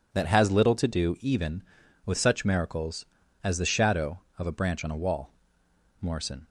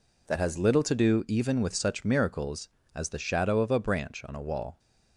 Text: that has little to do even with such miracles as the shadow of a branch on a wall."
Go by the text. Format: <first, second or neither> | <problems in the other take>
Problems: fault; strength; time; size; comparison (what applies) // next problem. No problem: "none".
second | goes on to say "Morrison"; slight; from 5.9 s on; 0.48 s long